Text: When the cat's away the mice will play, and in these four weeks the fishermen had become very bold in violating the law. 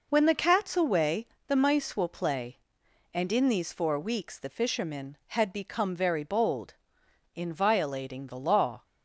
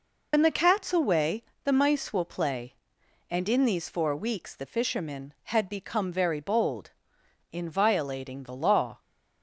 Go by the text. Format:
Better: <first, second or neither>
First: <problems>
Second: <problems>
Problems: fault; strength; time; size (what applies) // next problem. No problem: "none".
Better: first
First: pauses between "away" and "the"; slight; at 1.2 s; 0.20 s long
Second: loses the start of "When"; at 0.3 s; 65 ms // pauses between "away" and "the"; slight; at 1.4 s; 0.20 s long